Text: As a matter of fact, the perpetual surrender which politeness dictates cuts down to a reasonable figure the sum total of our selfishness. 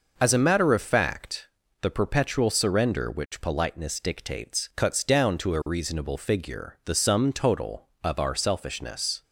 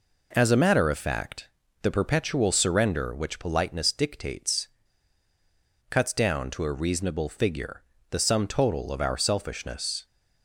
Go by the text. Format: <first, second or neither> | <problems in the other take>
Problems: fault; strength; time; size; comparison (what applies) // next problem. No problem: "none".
first | pauses between "dictates" and "cuts"; at 4.6 s; 1.1 s long // pauses between "figure" and "the"; slight; at 7.8 s; 0.30 s long